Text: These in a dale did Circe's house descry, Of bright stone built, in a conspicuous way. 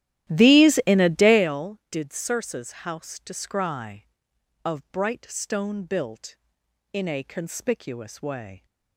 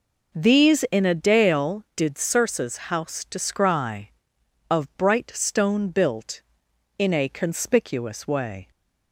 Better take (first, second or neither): second